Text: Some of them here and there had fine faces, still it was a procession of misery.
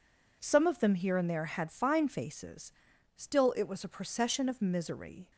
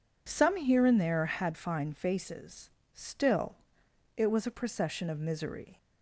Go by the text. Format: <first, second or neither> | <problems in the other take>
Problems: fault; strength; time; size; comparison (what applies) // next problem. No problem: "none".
first | skips "of them"; at 0.5 s // pauses between "still" and "it"; noticeable; at 3.5 s; 0.58 s long